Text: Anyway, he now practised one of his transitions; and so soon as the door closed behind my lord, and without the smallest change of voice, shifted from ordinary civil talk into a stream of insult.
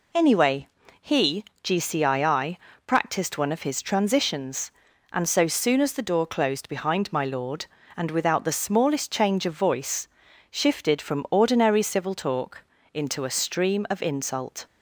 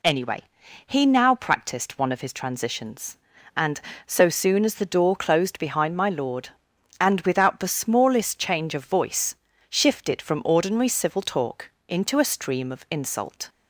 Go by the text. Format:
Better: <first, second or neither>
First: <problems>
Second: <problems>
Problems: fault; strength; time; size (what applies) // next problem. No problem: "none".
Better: second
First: says "gcii" for "now"; at 1.6 s // pauses between "talk" and "into"; slight; at 12.6 s; 0.28 s long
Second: pauses between "talk" and "into"; slight; at 11.7 s; 0.18 s long